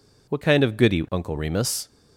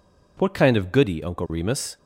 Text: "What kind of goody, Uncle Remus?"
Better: neither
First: none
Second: none

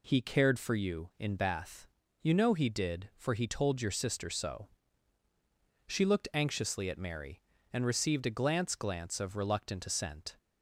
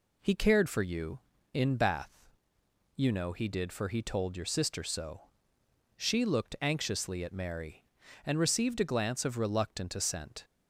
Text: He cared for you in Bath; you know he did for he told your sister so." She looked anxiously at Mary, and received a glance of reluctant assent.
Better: second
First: says "glance" twice; at 8.7 s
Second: none

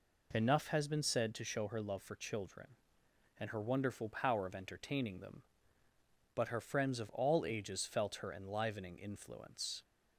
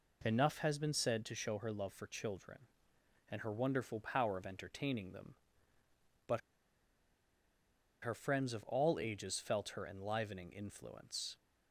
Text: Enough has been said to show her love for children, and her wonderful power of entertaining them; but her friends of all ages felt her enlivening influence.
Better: first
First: none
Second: pauses between "but" and "her"; strong; at 6.4 s; 1.6 s long

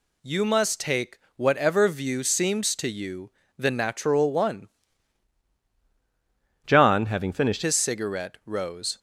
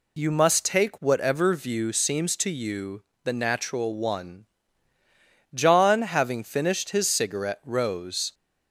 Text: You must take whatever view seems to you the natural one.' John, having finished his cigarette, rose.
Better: second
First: pauses between "take" and "whatever"; slight; at 1.1 s; 0.20 s long // pauses between "you" and "the"; slight; at 3.3 s; 0.26 s long // changes voice from "John" to "finished"; from 6.6 to 7.6 s; 1.0 s long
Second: pauses between "you" and "the"; slight; at 3.0 s; 0.20 s long

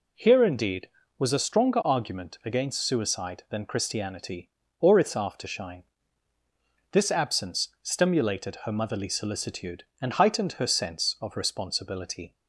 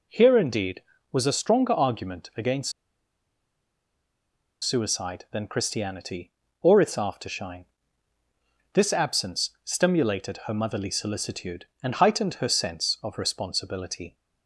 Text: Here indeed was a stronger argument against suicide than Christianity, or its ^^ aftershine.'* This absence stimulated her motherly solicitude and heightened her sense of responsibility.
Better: first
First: none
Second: pauses between "against" and "suicide"; strong; at 2.7 s; 1.9 s long

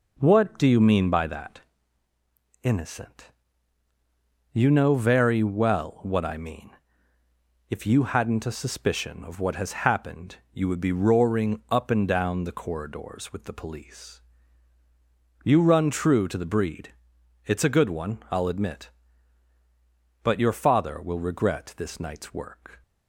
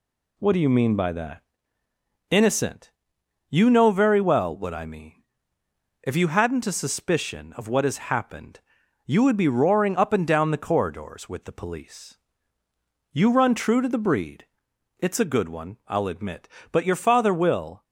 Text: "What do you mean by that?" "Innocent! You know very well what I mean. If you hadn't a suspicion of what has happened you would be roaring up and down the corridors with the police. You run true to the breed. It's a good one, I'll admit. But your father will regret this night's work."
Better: first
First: pauses between "happened" and "you"; slight; at 10.3 s; 0.18 s long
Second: pauses between "happened" and "you"; noticeable; at 8.5 s; 0.46 s long // stops before "regret this night's work"; at 17.8 s

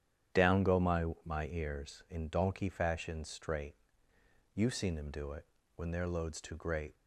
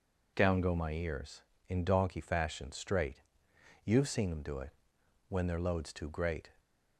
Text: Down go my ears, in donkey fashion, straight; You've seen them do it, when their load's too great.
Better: second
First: starts louder than the rest; strong; until 1.5 s; 10 dB // says "my" twice; at 1.2 s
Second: none

